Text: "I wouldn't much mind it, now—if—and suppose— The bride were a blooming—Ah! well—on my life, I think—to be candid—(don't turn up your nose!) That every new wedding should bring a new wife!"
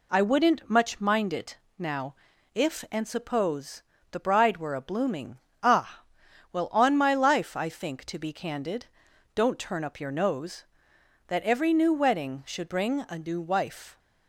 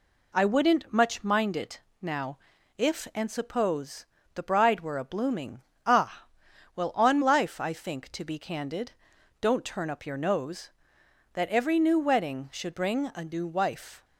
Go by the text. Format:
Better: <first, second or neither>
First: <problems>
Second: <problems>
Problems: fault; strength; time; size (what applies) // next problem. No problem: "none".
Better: first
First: none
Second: skips "my"; at 7.2 s